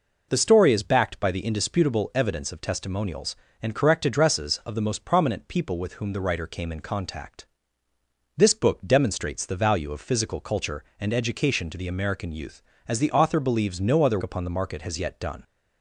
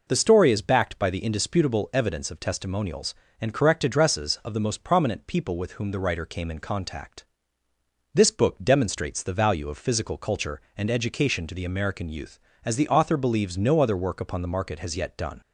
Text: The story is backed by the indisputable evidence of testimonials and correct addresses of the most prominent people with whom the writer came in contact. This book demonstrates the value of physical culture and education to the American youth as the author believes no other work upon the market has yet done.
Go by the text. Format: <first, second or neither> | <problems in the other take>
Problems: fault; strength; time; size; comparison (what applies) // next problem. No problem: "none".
second | skips "work"; at 14.2 s